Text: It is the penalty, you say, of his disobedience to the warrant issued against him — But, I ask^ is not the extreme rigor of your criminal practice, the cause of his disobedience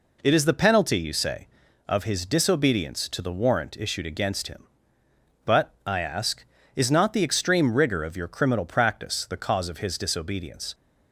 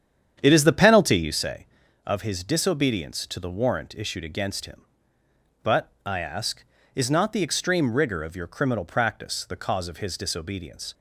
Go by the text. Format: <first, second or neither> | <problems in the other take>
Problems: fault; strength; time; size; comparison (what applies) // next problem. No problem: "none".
first | starts louder than the rest; strong; until 1.4 s; 8.5 dB